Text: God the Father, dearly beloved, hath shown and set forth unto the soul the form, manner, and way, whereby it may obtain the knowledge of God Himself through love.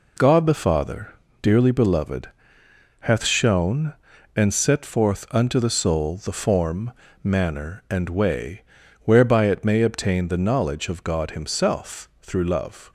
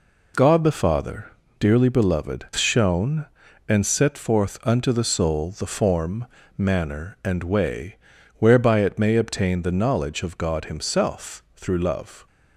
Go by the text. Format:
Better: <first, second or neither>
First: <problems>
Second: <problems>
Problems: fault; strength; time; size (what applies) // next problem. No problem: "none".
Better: first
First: none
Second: skips "hath"; at 2.5 s